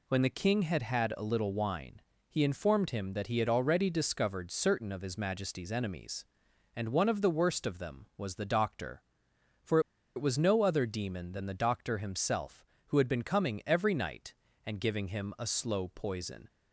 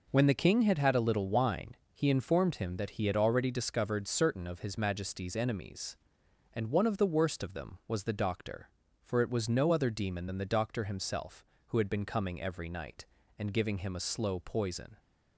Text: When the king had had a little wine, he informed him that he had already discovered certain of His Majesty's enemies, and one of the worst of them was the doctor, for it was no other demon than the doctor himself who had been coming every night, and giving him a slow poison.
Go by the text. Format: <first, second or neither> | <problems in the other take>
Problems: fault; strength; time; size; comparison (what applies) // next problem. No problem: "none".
second | pauses between "for" and "it"; at 9.7 s; 0.36 s long